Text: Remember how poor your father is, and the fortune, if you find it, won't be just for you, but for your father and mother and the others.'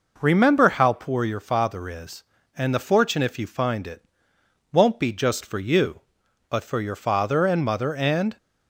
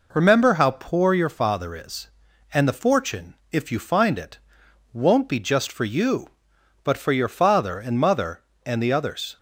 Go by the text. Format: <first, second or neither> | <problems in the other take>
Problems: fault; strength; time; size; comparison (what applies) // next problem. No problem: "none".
second | stops before "the others"; at 8.3 s